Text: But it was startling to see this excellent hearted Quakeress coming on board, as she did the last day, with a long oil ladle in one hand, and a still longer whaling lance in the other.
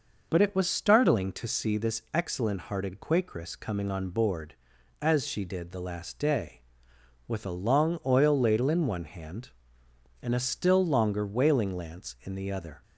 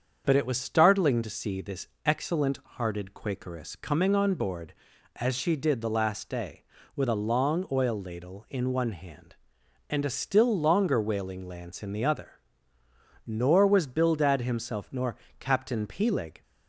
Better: first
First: none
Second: starts louder than the rest; strong; until 1.2 s; 7 dB // pauses between "this" and "excellent"; slight; at 1.8 s; 0.18 s long // goes on to say "Nor was Bildad himself nor Captain Peleg"; strong; from 13.2 s on; 3.1 s long

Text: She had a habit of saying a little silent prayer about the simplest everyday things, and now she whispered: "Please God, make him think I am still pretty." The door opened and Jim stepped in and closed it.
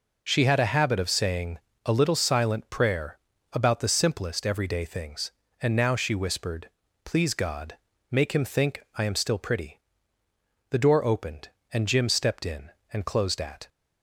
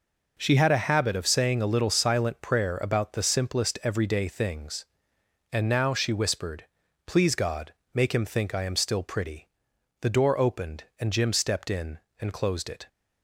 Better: second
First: pauses between "saying" and "a"; slight; at 1.5 s; 0.26 s long // pauses between "prayer" and "about"; slight; at 3.1 s; 0.34 s long // says "at" for "it"; at 13.4 s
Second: none

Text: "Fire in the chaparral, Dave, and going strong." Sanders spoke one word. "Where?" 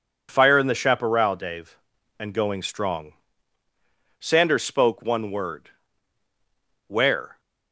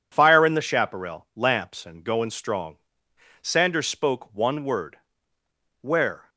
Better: first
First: none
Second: says "Lamps" for "Dave"; at 1.3 s

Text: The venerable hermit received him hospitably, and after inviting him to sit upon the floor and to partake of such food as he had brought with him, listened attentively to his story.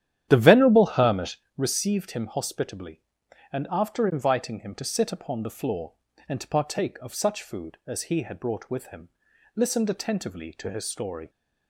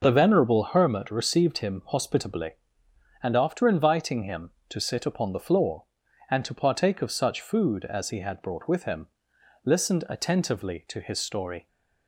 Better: second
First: starts louder than the rest; strong; until 1.5 s; 11 dB // pauses between "hermit" and "received"; slight; at 1.3 s; 0.22 s long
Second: none

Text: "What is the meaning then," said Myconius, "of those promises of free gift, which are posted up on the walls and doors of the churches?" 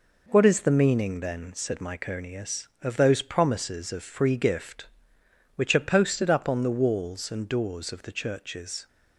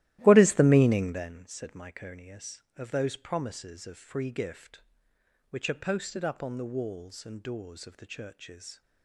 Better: first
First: none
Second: starts louder than the rest; strong; until 1.4 s; 15 dB

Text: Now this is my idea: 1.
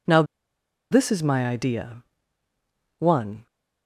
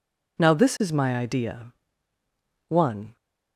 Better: second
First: pauses between "Now" and "this"; noticeable; at 0.2 s; 0.67 s long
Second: none

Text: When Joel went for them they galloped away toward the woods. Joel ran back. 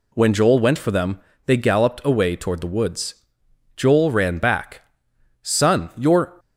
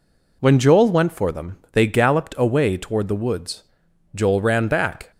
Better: second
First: pauses between "them" and "they"; slight; at 1.2 s; 0.26 s long // goes on to say "Son you're"; noticeable; from 5.4 s on; 0.98 s long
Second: none

